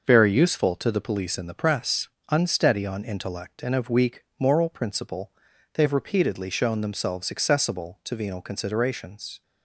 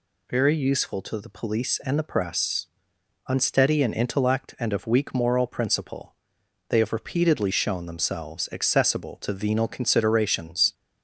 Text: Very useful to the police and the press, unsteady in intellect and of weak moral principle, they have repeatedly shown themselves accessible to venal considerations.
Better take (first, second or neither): second